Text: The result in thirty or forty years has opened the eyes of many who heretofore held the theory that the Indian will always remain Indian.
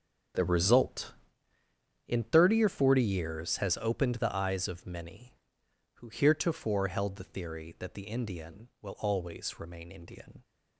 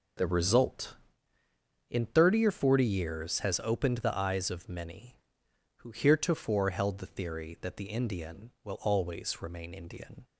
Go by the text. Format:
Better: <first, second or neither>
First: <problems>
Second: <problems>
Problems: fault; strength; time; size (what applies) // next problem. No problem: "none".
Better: second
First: gets quieter; strong; throughout; 13.5 dB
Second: none